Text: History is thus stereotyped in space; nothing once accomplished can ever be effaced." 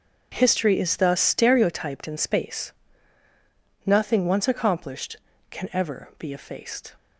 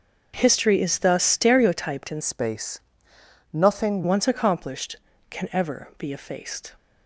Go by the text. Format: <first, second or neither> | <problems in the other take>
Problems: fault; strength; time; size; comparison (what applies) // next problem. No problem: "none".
first | starts louder than the rest; until 1.3 s; 6.5 dB // changes voice from "space" to "nothing"; from 2.2 to 4.0 s; 1.8 s long